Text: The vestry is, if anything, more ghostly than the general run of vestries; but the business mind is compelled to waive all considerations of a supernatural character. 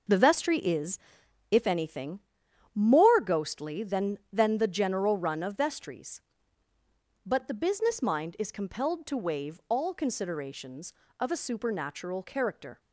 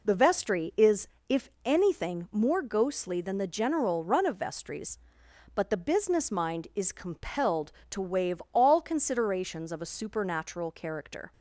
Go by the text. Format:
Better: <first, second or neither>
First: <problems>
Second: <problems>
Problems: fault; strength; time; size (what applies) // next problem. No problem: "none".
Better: second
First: says "than" twice; at 4.3 s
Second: none